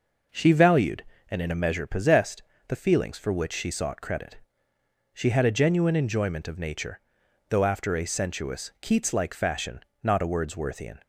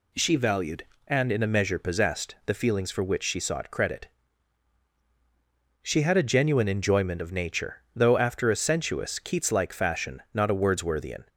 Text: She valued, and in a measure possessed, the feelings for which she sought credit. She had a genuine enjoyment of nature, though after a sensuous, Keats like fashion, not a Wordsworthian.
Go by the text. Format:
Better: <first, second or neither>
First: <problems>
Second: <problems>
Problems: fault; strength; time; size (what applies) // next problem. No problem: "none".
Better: neither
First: none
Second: none